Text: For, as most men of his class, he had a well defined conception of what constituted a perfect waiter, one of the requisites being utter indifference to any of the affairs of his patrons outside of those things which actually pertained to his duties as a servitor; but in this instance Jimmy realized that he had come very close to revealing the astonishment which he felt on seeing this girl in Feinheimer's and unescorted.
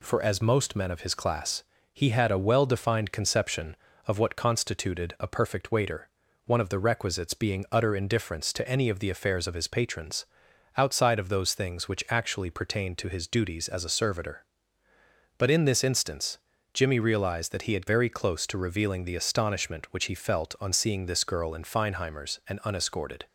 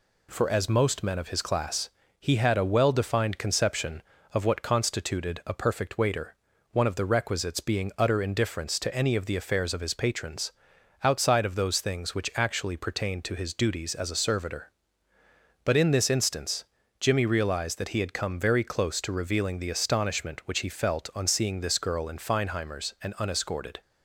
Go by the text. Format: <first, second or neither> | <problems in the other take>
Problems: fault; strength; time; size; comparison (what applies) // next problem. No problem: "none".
second | pauses between "patrons" and "outside"; noticeable; at 10.2 s; 0.52 s long; noticeable in the second // pauses between "instance" and "Jimmy"; slight; at 16.3 s; 0.36 s long; slight in the second // skips "come"; at 17.8 s